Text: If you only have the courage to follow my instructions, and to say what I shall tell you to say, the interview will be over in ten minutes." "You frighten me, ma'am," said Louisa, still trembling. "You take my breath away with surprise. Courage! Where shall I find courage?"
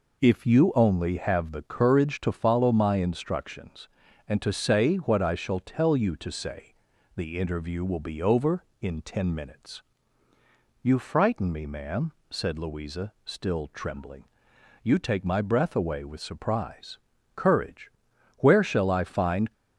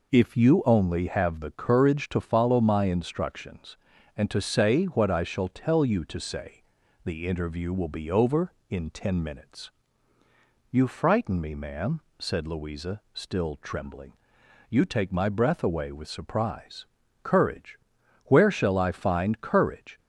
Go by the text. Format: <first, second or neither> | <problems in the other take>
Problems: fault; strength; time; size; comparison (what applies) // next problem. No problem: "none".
second | stops before "courage"; at 19.5 s